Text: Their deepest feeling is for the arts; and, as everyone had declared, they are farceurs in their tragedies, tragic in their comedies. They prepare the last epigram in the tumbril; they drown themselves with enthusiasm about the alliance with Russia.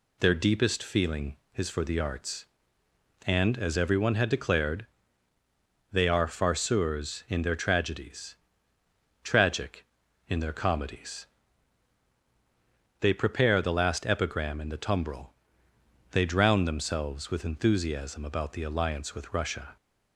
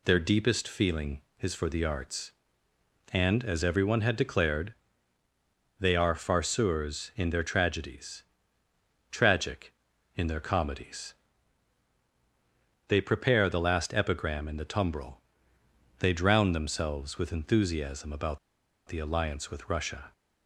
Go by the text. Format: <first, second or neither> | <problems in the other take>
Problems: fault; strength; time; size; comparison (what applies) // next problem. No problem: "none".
first | pauses between "about" and "the"; noticeable; at 18.3 s; 0.49 s long